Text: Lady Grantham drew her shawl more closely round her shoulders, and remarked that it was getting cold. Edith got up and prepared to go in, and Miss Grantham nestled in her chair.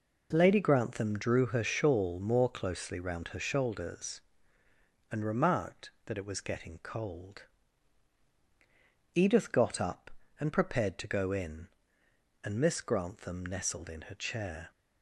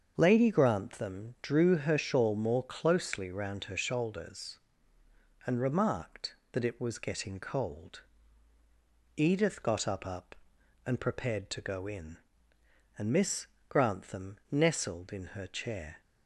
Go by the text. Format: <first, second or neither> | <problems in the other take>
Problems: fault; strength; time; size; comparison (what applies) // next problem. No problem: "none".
first | starts louder than the rest; until 1.1 s; 7 dB // says "up" twice; at 10.0 s // pauses between "Miss" and "Grantham"; slight; at 13.4 s; 0.22 s long